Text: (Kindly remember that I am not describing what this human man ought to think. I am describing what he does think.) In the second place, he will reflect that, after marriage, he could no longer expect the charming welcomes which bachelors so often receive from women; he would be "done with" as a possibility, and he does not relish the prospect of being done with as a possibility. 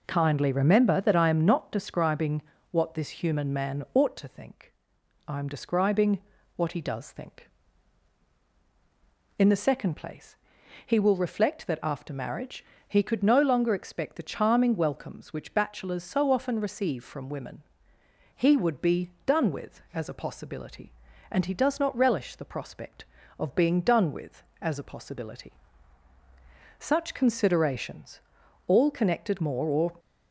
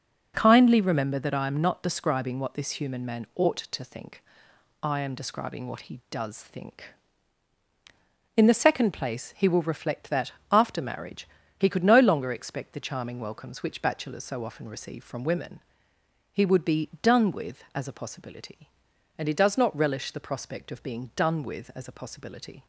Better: second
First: pauses between "describing" and "what"; slight; at 2.4 s; 0.28 s long // pauses between "describing" and "what"; slight; at 6.2 s; 0.32 s long // pauses between "be" and "done"; slight; at 19.0 s; 0.16 s long // goes on to say "Such considerations all connected more or"; strong; from 26.7 s on; 3.1 s long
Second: none

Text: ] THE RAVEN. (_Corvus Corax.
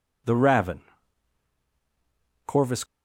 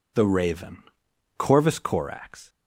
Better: second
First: stops before "Corax"; at 2.8 s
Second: none

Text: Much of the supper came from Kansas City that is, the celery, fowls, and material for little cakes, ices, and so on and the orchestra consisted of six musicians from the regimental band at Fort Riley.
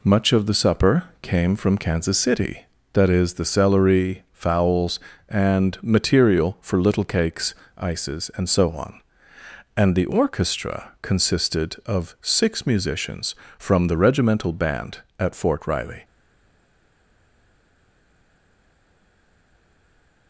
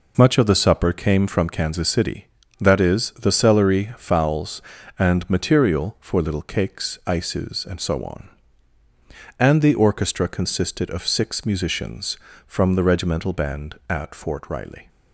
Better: second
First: pauses between "supper" and "came"; slight; at 1.0 s; 0.18 s long // stays silent after the last word; strong; from 16.0 s on; 4.2 s long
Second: none

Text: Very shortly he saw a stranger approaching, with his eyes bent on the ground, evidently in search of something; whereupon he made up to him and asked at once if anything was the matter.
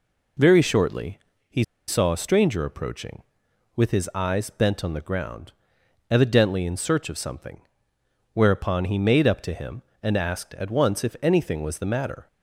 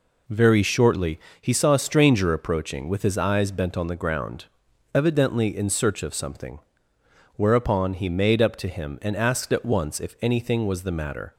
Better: second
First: pauses between "shortly" and "he"; slight; at 1.1 s; 0.32 s long // pauses between "he" and "saw"; slight; at 1.6 s; 0.24 s long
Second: pauses between "shortly" and "he"; slight; at 1.2 s; 0.20 s long

